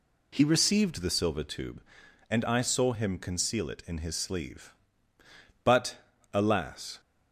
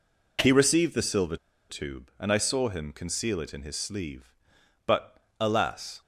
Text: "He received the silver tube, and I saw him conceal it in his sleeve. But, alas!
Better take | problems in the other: first | pauses between "silver" and "tube"; slight; at 1.3 s; 0.33 s long

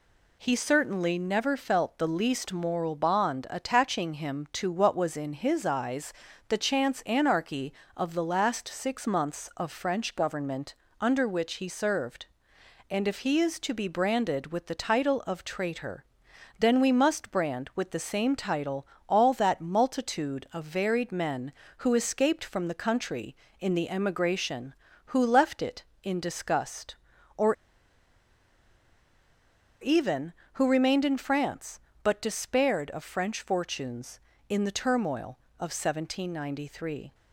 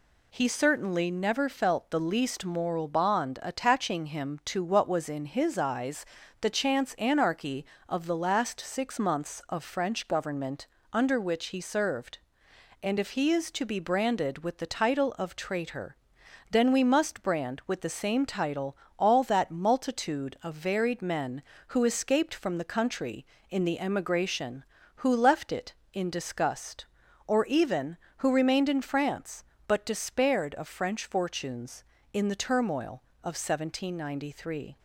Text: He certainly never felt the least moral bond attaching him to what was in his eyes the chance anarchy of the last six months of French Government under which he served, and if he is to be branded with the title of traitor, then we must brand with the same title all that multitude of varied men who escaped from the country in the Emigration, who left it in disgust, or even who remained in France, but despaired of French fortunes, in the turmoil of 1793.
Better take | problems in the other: second | pauses between "eyes" and "the"; slight; at 6.1 s; 0.34 s long; slight in the second // pauses between "Government" and "under"; slight; at 10.7 s; 0.26 s long; slight in the second // pauses between "title" and "all"; slight; at 18.8 s; 0.22 s long; slight in the second // pauses between "or" and "even"; strong; at 27.5 s; 2.2 s long

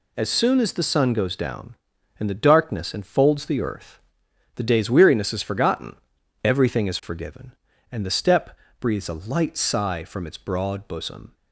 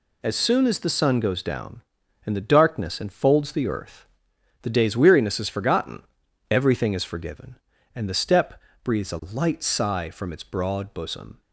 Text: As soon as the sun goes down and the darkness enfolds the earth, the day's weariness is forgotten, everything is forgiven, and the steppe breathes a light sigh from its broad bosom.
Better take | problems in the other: neither | pauses between "steppe" and "breathes"; slight; the same in both

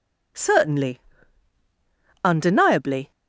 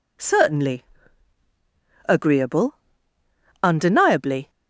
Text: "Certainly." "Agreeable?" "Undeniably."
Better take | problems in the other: second | skips "Agreeable"; at 1.6 s

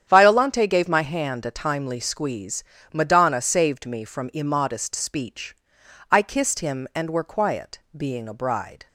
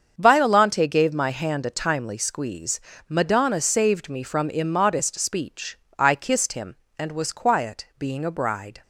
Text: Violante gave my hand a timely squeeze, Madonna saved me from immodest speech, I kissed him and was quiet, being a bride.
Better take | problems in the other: second | starts louder than the rest; strong; until 1.0 s; 9 dB; strong in the second // says "were" for "was"; at 7.0 s

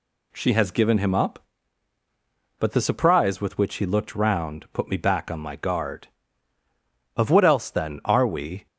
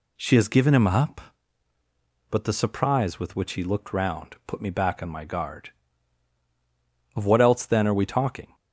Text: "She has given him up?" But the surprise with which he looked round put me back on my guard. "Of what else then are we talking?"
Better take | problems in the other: second | stops before "talking"; at 8.6 s

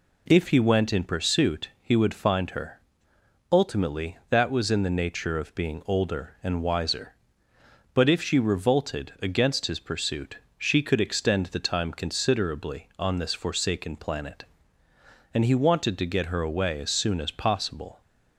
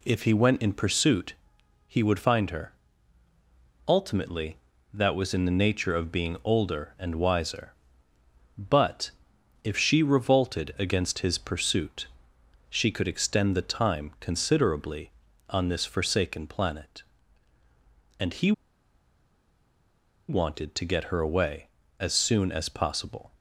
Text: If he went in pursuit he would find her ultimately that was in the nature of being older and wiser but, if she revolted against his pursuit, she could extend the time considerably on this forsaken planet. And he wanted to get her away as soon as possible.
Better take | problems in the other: first | pauses between "pursuit" and "he"; noticeable; at 1.3 s; 0.54 s long // pauses between "her" and "ultimately"; at 2.7 s; 1.1 s long; noticeable in the first // pauses between "he" and "wanted"; strong; at 18.5 s; 1.7 s long

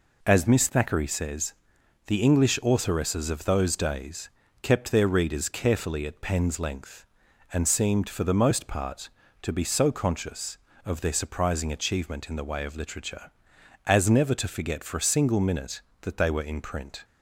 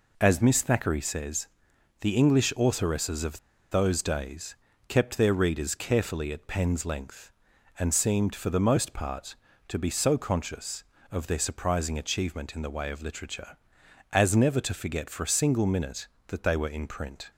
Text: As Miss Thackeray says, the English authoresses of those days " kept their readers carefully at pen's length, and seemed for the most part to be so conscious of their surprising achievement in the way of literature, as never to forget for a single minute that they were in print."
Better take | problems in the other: first | pauses between "of" and "those"; slight; at 3.3 s; 0.33 s long

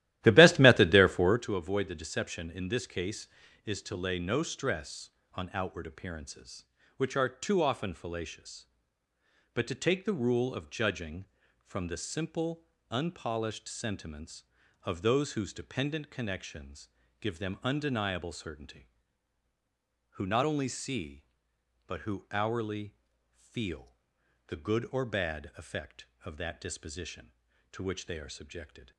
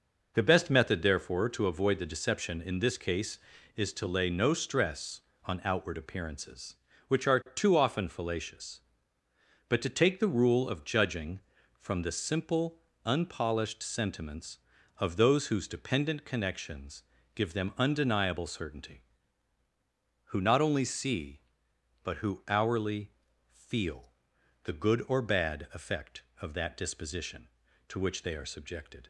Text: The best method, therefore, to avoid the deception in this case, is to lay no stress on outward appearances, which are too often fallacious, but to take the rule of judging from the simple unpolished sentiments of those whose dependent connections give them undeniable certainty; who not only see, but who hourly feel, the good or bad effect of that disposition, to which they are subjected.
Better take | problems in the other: second | starts louder than the rest; strong; until 1.4 s; 14.5 dB // pauses between "simple" and "unpolished"; slight; at 12.6 s; 0.26 s long; slight in the second // pauses between "connections" and "give"; slight; at 16.8 s; 0.30 s long; slight in the second // pauses between "hourly" and "feel"; at 22.9 s; 0.38 s long; also in the second

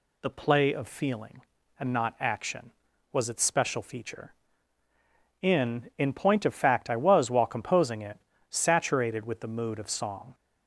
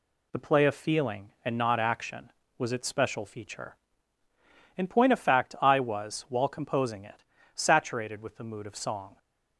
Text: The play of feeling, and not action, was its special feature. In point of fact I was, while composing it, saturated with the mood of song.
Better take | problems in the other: second | says "In" twice; at 5.9 s

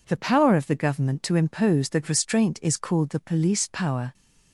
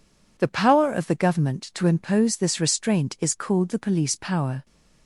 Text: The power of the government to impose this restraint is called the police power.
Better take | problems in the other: second | says "that" for "this"; at 1.8 s

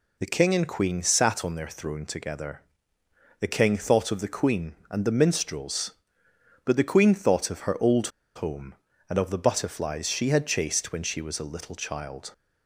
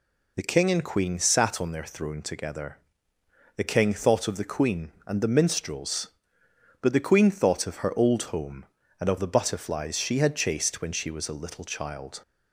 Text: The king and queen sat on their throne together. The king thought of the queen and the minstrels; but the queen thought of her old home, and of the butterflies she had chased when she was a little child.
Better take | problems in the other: second | pauses between "old" and "home"; slight; at 8.0 s; 0.27 s long

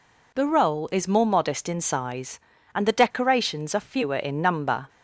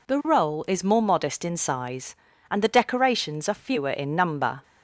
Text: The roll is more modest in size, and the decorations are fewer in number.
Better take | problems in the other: neither | none

